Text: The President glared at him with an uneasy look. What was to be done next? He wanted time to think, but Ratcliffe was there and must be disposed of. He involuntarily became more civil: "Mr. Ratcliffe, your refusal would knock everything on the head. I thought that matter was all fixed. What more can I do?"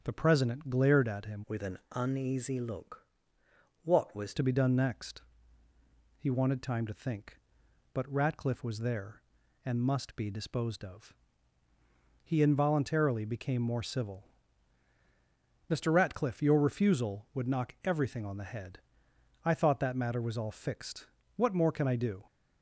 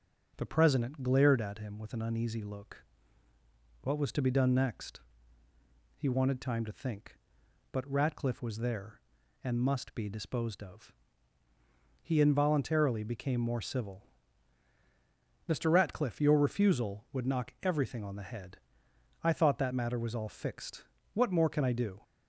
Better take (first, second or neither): second